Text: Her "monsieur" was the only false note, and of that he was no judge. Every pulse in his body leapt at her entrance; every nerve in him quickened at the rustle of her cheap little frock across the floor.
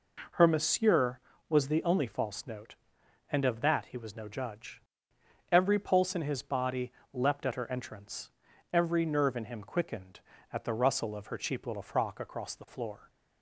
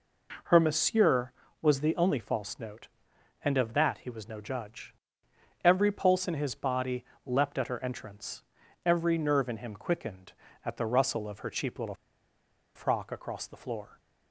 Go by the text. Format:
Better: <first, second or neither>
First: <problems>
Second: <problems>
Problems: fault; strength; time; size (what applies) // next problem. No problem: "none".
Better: first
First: pauses between "body" and "leapt"; slight; at 6.9 s; 0.20 s long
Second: pauses between "body" and "leapt"; slight; at 7.0 s; 0.20 s long // pauses between "little" and "frock"; noticeable; at 11.9 s; 0.80 s long